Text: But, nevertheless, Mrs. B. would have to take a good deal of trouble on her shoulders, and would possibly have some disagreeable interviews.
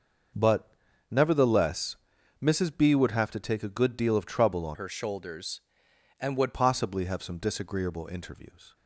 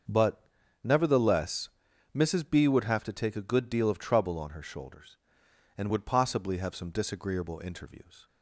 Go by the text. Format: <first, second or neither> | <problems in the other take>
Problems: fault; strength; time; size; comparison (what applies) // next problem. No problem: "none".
second | starts louder than the rest; until 1.7 s; 6 dB; also in the second // changes voice from "her" to "would"; from 4.7 to 6.5 s; 1.8 s long